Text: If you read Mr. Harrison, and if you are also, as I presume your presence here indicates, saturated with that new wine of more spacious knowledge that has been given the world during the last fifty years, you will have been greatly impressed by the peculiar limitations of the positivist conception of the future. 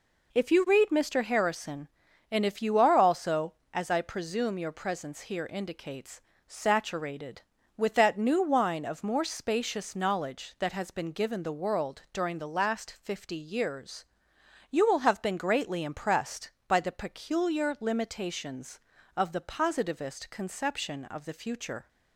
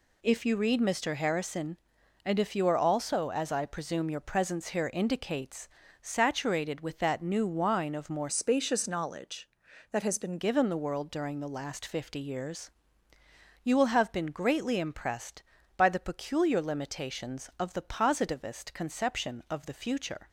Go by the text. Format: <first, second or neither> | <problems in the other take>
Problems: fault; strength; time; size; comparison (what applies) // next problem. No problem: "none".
first | changes voice from "spacious" to "been"; from 8.2 to 10.3 s; 2.1 s long